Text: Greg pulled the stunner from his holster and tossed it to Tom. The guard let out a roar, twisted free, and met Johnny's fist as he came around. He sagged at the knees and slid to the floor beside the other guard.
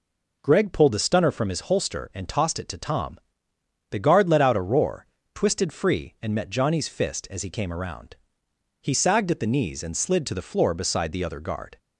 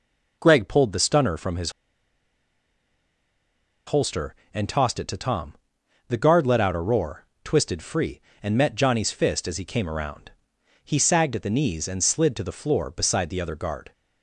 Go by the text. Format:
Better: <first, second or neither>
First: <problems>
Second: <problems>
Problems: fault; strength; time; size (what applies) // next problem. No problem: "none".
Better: first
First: none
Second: pauses between "his" and "holster"; strong; at 1.7 s; 2.1 s long